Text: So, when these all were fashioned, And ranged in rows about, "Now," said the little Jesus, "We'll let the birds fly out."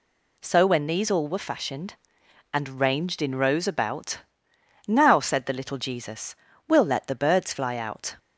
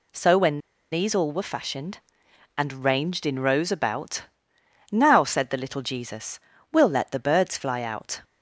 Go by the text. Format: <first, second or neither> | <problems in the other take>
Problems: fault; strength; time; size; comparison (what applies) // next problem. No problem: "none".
first | pauses between "when" and "these"; slight; at 0.5 s; 0.34 s long